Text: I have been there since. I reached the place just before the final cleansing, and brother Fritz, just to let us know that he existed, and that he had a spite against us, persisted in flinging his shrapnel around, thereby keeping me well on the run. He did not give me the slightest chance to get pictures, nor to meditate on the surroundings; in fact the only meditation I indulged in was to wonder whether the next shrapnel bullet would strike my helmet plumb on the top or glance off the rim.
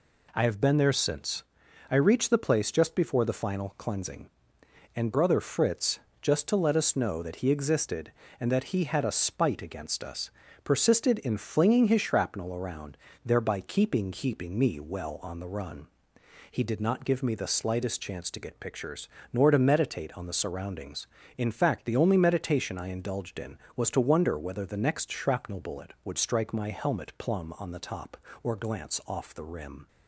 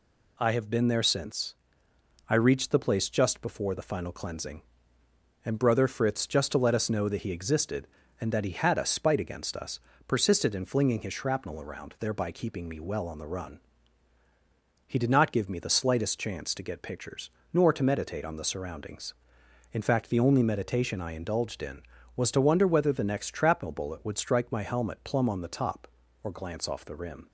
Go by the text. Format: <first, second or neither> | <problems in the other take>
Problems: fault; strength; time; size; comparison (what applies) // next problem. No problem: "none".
second | says "keeping" twice; at 14.1 s